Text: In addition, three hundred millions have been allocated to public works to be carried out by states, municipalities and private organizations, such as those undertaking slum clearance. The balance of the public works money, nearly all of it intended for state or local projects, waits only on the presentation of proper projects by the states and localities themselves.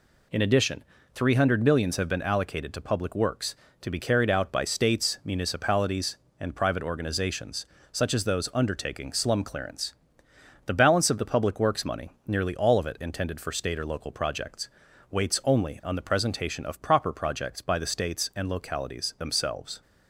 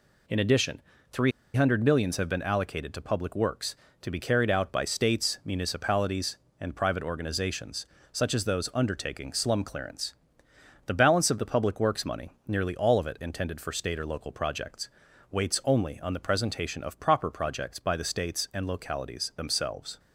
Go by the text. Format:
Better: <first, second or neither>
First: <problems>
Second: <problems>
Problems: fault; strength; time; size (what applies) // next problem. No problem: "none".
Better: first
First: none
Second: pauses between "three" and "hundred"; slight; at 1.3 s; 0.23 s long